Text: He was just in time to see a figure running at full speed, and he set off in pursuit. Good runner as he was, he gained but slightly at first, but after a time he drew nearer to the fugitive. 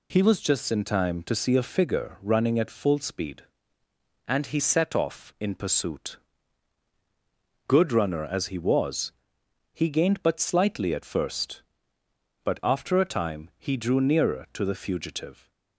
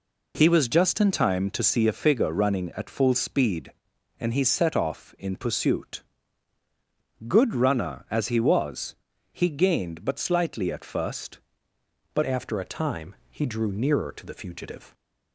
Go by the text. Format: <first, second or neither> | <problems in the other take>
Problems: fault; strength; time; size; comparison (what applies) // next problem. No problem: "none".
first | changes voice at "after"; from 12.2 s on; 2.7 s long // pauses between "time" and "he"; slight; at 13.1 s; 0.16 s long